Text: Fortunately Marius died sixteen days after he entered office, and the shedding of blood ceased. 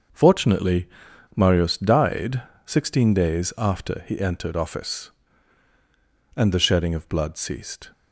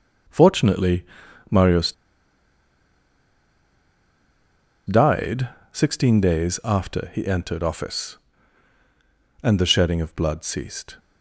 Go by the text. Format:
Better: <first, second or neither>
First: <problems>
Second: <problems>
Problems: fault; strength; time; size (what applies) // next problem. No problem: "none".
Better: first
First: starts louder than the rest; until 1.6 s; 6 dB // pauses between "Fortunately" and "Marius"; noticeable; at 0.8 s; 0.48 s long // pauses between "died" and "sixteen"; slight; at 2.4 s; 0.24 s long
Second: starts louder than the rest; noticeable; until 1.7 s; 6 dB // pauses between "Fortunately" and "Marius"; noticeable; at 1.0 s; 0.46 s long // pauses between "Marius" and "died"; strong; at 1.9 s; 2.9 s long // pauses between "died" and "sixteen"; slight; at 5.4 s; 0.24 s long